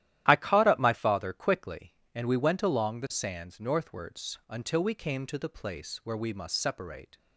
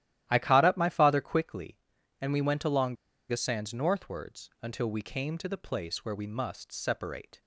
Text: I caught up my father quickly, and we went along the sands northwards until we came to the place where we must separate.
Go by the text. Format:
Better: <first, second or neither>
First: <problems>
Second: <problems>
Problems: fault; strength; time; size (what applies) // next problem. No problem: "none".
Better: first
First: starts louder than the rest; strong; until 1.2 s; 12.5 dB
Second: starts louder than the rest; strong; until 1.3 s; 13 dB // pauses between "along" and "the"; slight; at 2.9 s; 0.34 s long